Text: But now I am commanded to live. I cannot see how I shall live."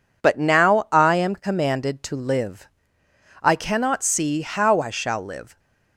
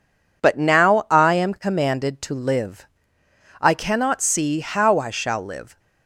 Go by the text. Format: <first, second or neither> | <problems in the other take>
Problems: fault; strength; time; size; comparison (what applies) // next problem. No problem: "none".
neither | none